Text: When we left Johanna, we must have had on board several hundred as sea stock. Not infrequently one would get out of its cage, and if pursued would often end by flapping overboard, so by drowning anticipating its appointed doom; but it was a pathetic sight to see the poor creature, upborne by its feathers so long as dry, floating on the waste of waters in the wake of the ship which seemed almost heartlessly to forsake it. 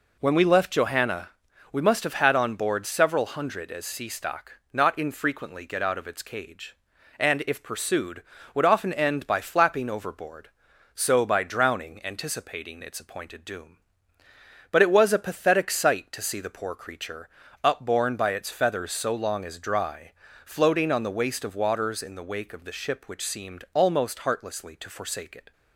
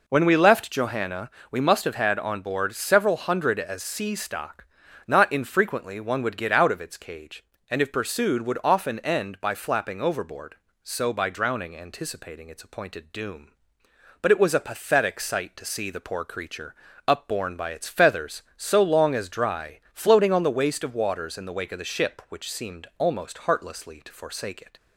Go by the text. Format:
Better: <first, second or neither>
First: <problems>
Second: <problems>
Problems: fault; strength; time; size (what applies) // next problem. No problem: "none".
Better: second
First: skips "one would"; at 5.6 s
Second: none